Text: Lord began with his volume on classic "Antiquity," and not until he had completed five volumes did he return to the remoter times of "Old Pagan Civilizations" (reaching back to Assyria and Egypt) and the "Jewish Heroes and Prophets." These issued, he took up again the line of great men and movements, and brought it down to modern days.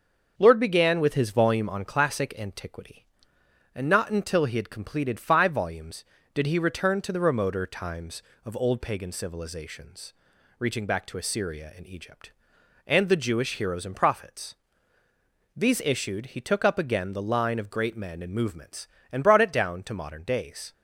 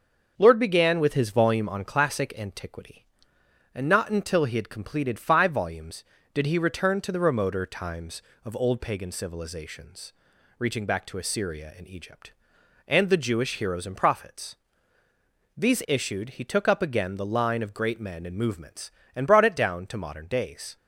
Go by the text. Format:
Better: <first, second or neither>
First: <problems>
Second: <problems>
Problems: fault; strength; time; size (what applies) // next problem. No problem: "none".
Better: neither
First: starts louder than the rest; until 1.3 s; 6.5 dB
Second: starts louder than the rest; until 1.3 s; 6.5 dB